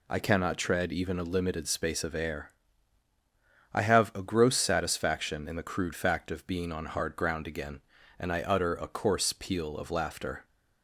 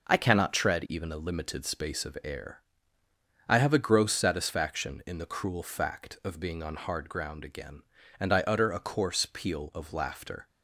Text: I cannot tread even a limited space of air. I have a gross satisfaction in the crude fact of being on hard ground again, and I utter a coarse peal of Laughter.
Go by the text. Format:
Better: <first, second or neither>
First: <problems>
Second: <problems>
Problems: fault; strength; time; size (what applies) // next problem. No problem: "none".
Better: first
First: none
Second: says "cruel" for "crude"; at 5.2 s